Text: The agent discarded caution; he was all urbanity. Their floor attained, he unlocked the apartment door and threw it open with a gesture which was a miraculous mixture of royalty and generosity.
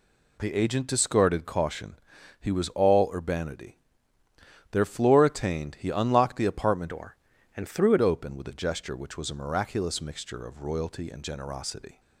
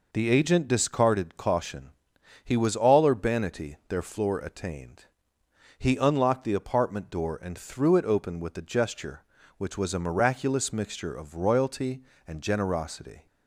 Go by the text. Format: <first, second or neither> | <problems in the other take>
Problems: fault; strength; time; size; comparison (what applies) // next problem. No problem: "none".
second | changes voice from "door" to "it"; from 6.8 to 7.9 s; 1.1 s long